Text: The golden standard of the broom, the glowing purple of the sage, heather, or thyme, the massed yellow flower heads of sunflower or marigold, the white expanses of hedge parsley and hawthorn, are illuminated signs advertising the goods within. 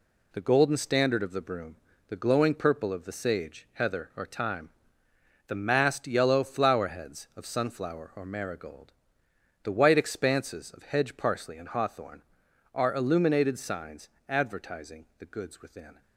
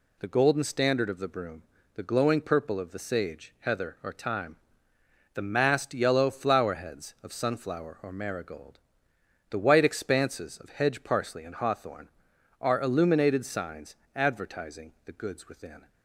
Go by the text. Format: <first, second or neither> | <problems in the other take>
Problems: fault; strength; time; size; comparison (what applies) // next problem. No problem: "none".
second | gets quieter; throughout; 6.5 dB // pauses between "signs" and "advertising"; slight; at 14.0 s; 0.22 s long; slight in the second